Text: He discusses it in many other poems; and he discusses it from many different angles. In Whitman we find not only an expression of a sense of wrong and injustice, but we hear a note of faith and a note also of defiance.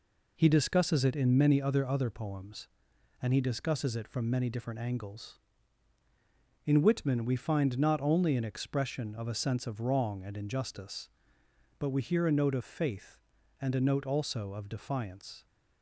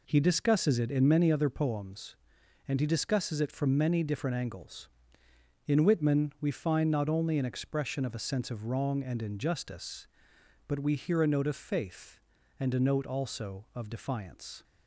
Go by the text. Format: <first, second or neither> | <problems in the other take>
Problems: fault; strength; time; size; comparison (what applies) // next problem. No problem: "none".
second | says "other" twice; at 1.8 s